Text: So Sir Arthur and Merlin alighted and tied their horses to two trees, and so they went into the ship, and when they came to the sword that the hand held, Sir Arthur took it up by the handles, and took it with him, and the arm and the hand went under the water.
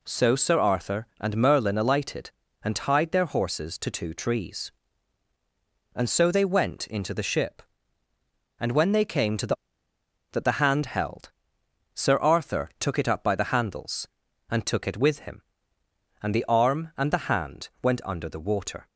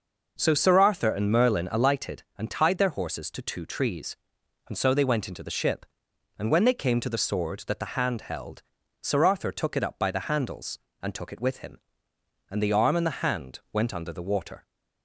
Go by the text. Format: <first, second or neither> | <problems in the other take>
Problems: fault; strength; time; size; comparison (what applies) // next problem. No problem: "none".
second | skips "sword"; at 9.9 s